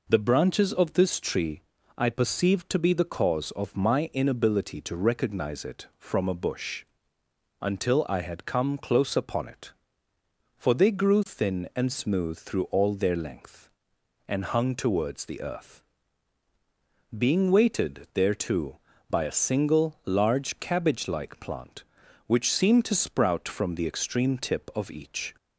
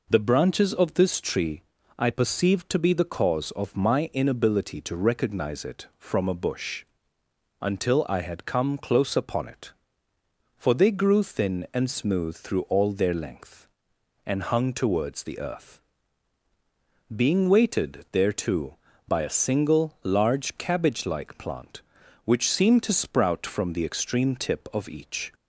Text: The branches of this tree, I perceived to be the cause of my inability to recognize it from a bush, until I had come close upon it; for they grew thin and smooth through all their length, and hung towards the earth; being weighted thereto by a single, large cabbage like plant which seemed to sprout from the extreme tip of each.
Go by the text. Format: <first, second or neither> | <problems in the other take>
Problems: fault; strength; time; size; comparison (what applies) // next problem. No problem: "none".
neither | none